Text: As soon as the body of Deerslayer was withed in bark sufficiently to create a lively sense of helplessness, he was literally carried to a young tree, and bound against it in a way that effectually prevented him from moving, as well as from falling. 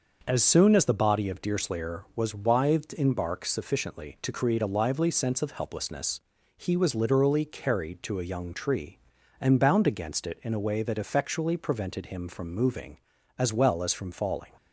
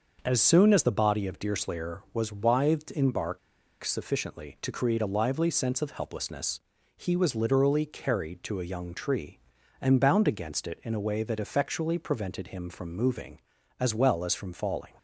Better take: first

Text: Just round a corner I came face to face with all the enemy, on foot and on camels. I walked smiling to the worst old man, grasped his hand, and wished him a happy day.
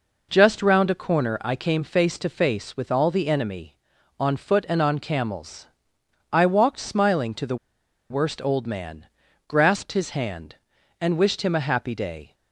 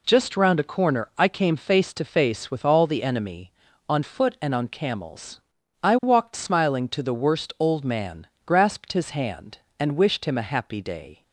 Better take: second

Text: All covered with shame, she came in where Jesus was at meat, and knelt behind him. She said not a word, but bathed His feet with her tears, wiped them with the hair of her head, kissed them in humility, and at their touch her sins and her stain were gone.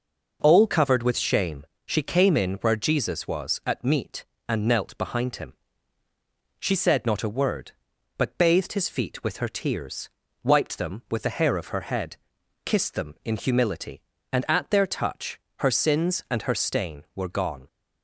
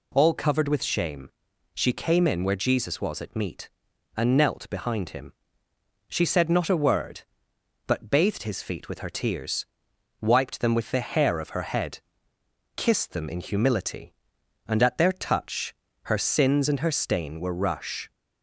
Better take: first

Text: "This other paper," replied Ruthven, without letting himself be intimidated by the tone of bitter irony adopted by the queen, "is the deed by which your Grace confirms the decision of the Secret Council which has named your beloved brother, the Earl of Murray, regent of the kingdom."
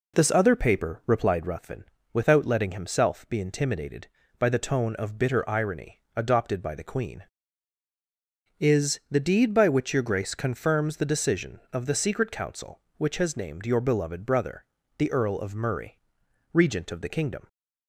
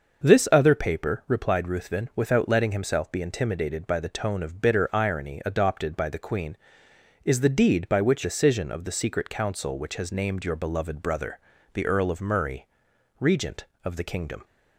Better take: first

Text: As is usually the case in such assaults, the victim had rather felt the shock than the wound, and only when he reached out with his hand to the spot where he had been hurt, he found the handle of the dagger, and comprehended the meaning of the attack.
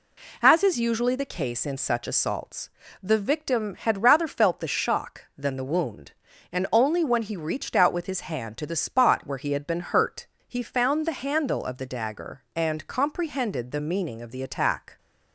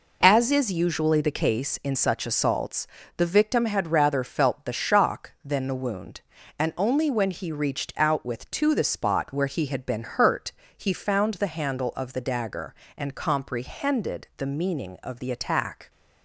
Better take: first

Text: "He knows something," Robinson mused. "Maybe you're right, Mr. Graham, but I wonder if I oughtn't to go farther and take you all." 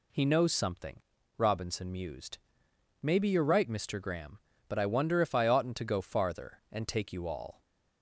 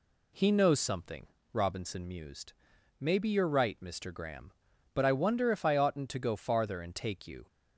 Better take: first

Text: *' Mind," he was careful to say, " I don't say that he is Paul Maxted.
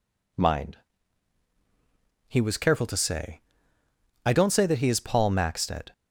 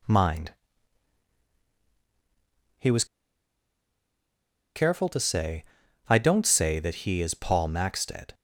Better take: first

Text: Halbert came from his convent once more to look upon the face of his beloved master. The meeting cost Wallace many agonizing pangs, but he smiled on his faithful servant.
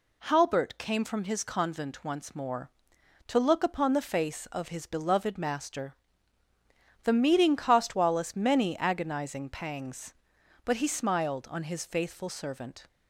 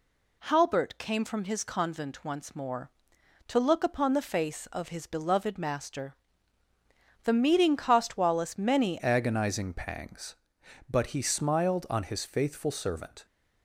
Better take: first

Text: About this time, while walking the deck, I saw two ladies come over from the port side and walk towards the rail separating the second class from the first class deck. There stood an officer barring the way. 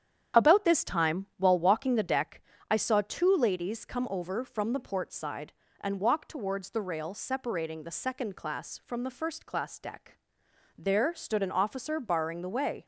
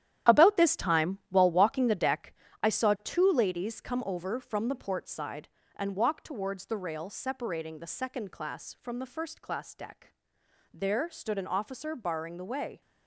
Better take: first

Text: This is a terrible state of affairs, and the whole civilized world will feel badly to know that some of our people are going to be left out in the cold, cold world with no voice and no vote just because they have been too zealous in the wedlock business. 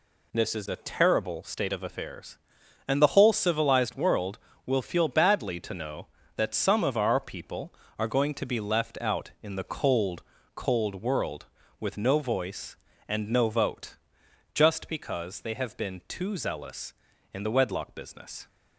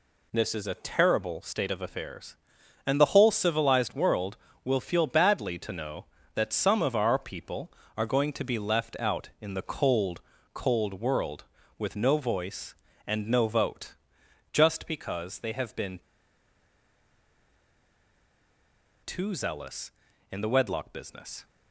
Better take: first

